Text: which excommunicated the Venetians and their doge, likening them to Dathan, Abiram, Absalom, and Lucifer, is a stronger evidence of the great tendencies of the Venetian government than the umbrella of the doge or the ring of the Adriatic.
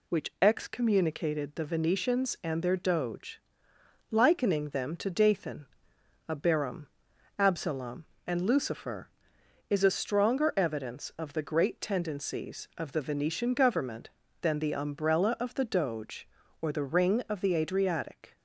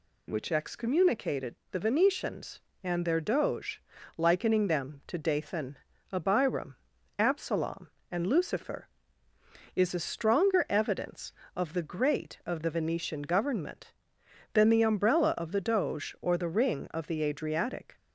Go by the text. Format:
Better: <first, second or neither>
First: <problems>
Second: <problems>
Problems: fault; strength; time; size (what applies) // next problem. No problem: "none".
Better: first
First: none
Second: pauses between "excommunicated" and "the"; slight; at 1.5 s; 0.16 s long // skips "tendencies"; at 12.4 s